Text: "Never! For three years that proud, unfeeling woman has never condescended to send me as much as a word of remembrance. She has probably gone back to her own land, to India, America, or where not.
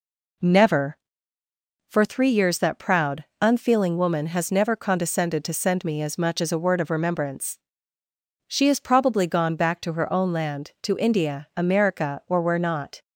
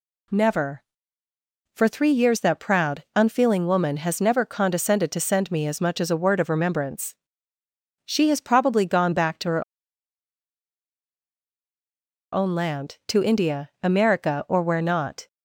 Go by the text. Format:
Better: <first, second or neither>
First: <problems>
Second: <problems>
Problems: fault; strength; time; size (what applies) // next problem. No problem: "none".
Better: first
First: none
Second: pauses between "her" and "own"; strong; at 9.6 s; 2.7 s long